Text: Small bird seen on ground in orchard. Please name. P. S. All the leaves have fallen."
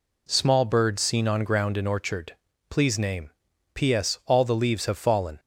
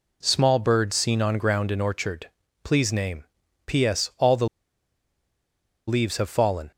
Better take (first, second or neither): first